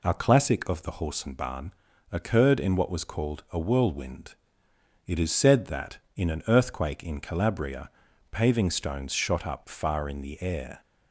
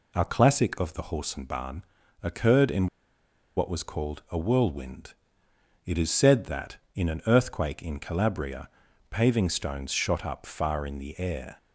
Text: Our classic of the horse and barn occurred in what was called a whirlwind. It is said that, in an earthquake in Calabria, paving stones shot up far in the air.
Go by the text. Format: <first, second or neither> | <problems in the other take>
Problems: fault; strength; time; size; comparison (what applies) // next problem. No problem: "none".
first | pauses between "barn" and "occurred"; at 1.8 s; 0.40 s long; also in the first // pauses between "in" and "what"; noticeable; at 2.8 s; 0.69 s long